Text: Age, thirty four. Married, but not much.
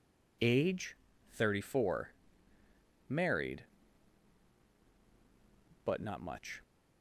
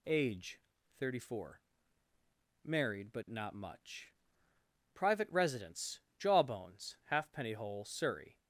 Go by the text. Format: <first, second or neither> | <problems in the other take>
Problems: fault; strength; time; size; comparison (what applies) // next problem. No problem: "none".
first | goes on to say "Private residence Jawbones Halfpenny Hole Surrey"; strong; from 4.9 s on; 3.4 s long